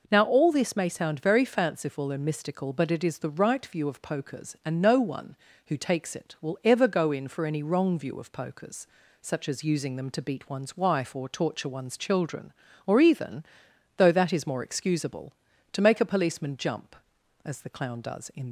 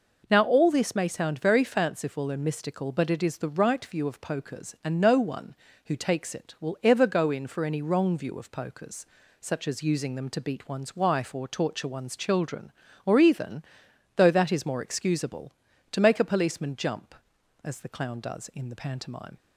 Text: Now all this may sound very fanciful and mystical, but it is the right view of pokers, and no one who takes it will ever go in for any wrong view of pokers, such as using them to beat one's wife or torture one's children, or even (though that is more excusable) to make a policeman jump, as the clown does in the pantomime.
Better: second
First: stops before "the pantomime"; at 18.4 s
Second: none

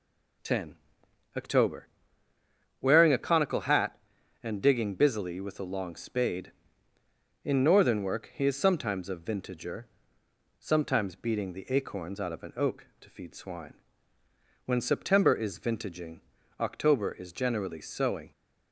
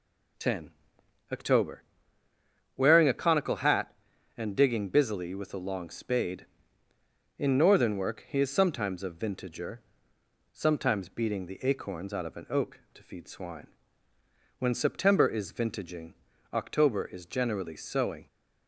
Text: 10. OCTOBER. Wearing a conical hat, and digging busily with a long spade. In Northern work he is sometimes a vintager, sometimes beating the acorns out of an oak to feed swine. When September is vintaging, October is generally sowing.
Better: neither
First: none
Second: none

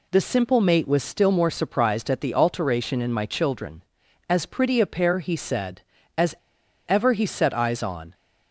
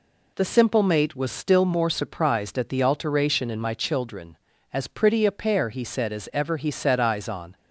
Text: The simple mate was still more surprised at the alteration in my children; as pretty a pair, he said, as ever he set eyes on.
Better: second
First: pauses between "as" and "ever"; noticeable; at 6.3 s; 0.53 s long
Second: none

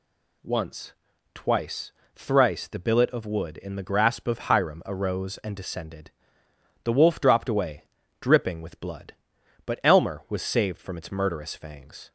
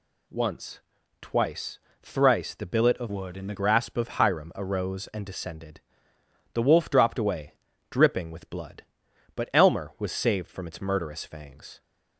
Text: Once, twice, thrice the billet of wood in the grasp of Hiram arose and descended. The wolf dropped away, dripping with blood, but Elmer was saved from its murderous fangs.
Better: first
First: none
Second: changes voice from "wood" to "the"; from 3.0 to 3.5 s; 0.5 s long

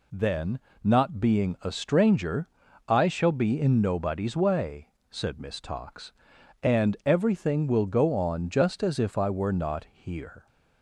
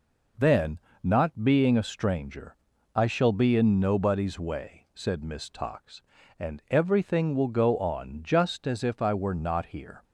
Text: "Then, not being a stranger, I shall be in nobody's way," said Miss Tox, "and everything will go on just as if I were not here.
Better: neither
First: none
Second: none

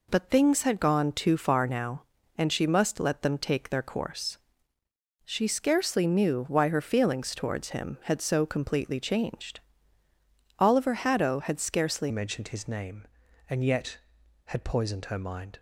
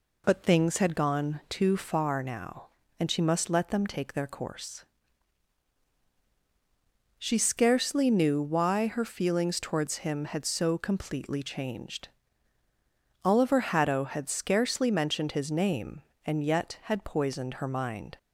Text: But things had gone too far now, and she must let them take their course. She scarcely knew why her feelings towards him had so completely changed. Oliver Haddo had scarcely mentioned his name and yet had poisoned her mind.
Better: second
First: changes voice at "mentioned"; from 12.0 s on; 3.5 s long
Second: none

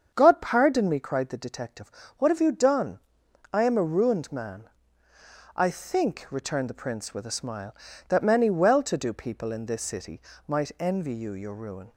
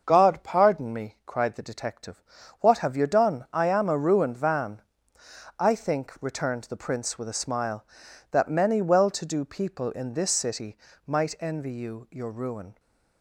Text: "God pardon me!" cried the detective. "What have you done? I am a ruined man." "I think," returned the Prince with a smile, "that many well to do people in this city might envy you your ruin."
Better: first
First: starts louder than the rest; strong; until 1.1 s; 7 dB // pauses between "city" and "might"; slight; at 10.2 s; 0.26 s long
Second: starts louder than the rest; until 1.0 s; 6 dB // says "van" for "man"; at 4.3 s // pauses between "city" and "might"; slight; at 10.7 s; 0.30 s long

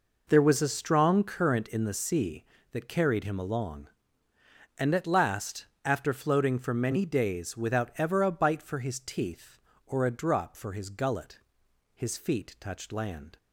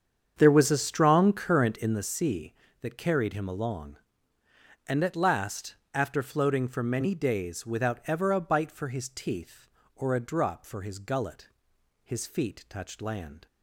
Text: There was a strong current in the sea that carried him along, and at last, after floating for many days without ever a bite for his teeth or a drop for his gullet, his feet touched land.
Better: first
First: none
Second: starts louder than the rest; strong; until 2.1 s; 7.5 dB

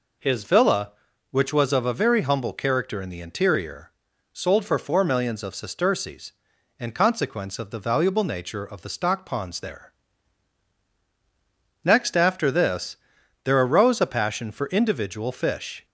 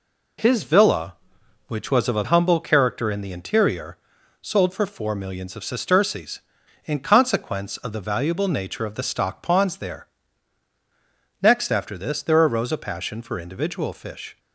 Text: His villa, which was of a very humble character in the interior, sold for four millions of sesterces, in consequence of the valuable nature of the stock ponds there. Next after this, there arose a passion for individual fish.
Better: first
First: none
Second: skips "very"; at 2.2 s

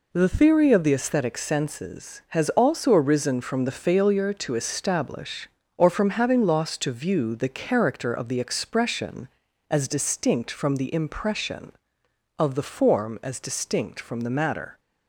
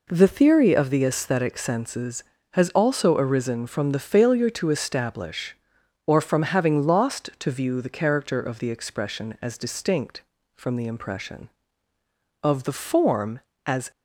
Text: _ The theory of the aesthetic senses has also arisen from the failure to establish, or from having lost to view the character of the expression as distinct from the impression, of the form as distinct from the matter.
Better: first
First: none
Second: stops before "distinct from the matter"; at 13.9 s

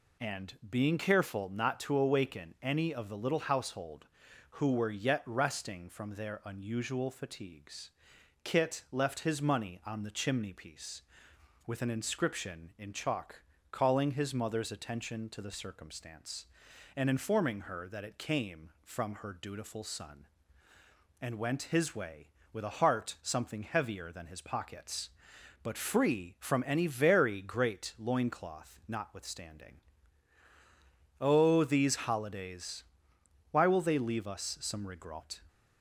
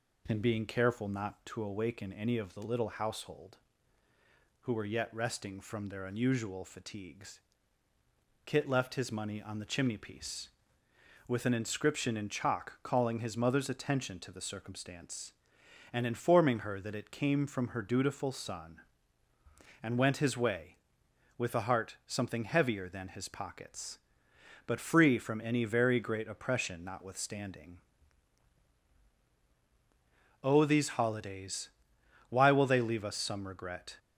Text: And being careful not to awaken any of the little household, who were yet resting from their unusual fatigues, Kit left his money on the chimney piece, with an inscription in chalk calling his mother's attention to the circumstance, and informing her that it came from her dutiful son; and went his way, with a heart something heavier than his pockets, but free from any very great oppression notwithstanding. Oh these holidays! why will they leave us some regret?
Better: second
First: pauses between "chalk" and "calling"; slight; at 13.4 s; 0.30 s long // says "loincloth" for "oppression"; at 27.9 s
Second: none

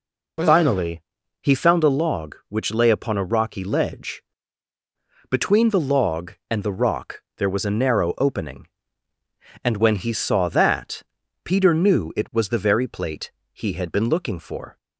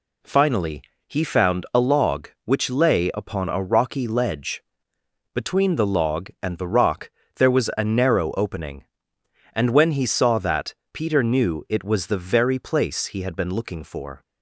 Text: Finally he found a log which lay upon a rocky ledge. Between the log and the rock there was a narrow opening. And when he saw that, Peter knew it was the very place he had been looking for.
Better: second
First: pauses between "Finally" and "he"; at 1.0 s; 0.40 s long // pauses between "rock" and "there"; slight; at 7.2 s; 0.16 s long // says "plate" for "place"; at 12.8 s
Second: pauses between "Finally" and "he"; slight; at 0.8 s; 0.26 s long // pauses between "rock" and "there"; slight; at 7.0 s; 0.26 s long

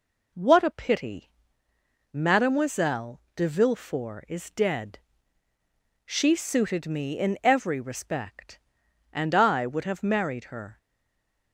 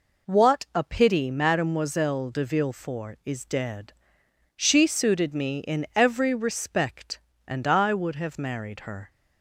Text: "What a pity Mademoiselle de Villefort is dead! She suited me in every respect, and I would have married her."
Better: second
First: pauses between "pity" and "Mademoiselle"; noticeable; at 1.2 s; 0.84 s long // pauses between "Mademoiselle" and "de"; slight; at 3.1 s; 0.16 s long // stays silent after the last word; slight; from 10.7 s on; 0.8 s long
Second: none

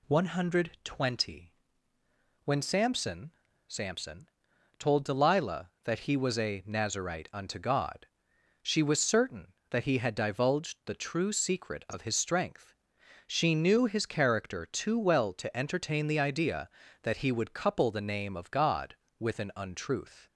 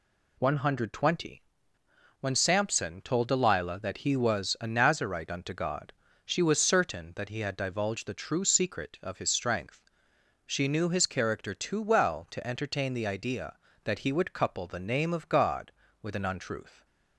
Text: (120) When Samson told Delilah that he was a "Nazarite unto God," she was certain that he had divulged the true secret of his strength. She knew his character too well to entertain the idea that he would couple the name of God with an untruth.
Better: second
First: says "Samson" twice; at 3.6 s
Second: none

